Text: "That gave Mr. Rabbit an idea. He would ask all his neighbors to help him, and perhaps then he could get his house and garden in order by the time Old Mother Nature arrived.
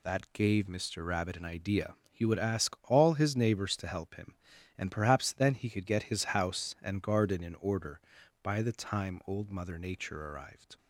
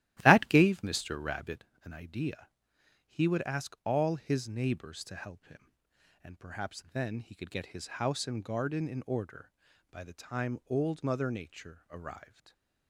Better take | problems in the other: first | starts louder than the rest; strong; until 1.6 s; 14.5 dB // pauses between "Rabbit" and "an"; slight; at 1.6 s; 0.20 s long // stays silent after the last word; slight; from 12.2 s on; 0.6 s long

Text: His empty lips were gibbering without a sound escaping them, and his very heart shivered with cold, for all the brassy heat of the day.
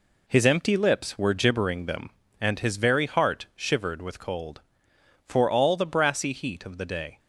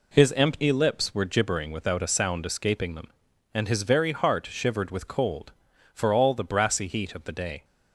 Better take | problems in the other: second | skips "without a sound escaping"; at 1.8 s

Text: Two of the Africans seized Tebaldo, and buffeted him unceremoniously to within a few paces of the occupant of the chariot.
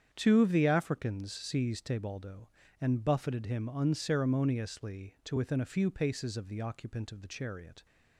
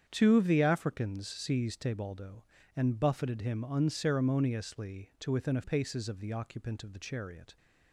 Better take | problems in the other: first | starts louder than the rest; strong; until 1.0 s; 8 dB; strong in the first // skips "few"; at 5.6 s

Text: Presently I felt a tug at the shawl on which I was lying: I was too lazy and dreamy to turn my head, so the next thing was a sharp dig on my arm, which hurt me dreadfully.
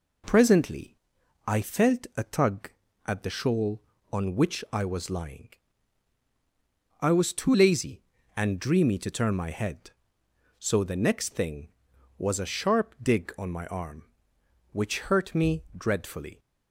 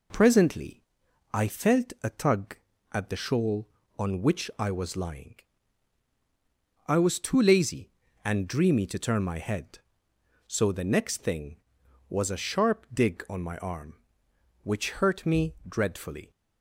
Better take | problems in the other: neither | pauses between "Presently" and "I"; noticeable; the same in both

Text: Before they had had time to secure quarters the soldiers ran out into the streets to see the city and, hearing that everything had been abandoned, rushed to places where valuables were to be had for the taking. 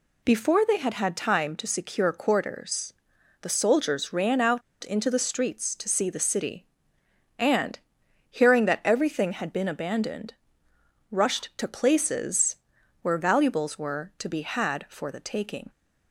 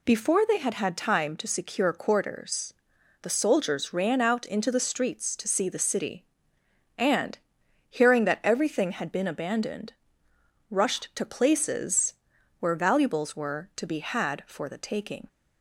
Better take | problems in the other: second | pauses between "quarters" and "the"; noticeable; at 2.9 s; 0.48 s long; noticeable in the second // pauses between "out" and "into"; slight; at 4.6 s; 0.22 s long // pauses between "places" and "where"; noticeable; at 12.5 s; 0.46 s long; noticeable in the second

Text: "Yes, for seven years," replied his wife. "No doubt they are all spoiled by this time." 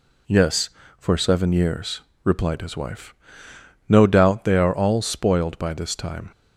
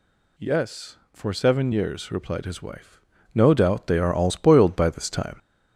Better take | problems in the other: first | gets louder; throughout; 3.5 dB

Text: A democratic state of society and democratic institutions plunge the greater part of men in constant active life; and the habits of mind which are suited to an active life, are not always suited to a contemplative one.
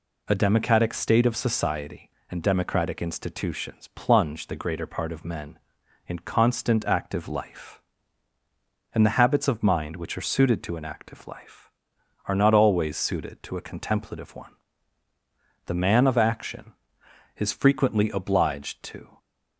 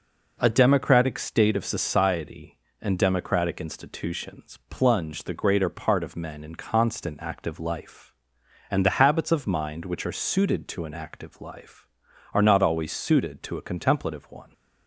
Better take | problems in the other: second | goes on to say "The man of action is frequently obliged to"; strong; from 15.6 s on; 3.5 s long

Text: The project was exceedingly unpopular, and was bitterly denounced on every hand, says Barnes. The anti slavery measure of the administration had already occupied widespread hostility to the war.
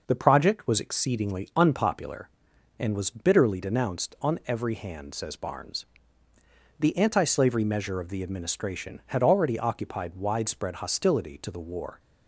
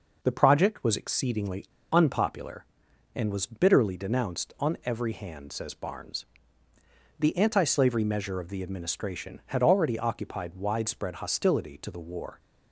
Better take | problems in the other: first | pauses between "exceedingly" and "unpopular"; slight; at 1.6 s; 0.25 s long

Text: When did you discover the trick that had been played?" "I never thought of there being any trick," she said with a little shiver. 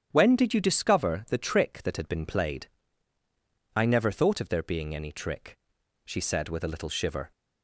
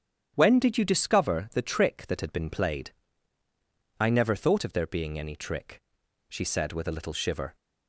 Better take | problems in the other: neither | starts louder than the rest; strong; the same in both

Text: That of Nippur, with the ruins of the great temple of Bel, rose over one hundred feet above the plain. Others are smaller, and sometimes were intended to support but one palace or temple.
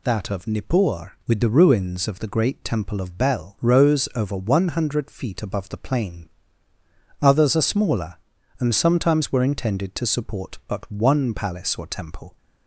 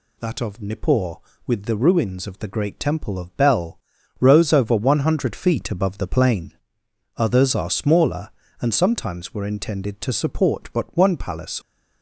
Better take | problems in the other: first | stops before "or temple"; at 11.6 s

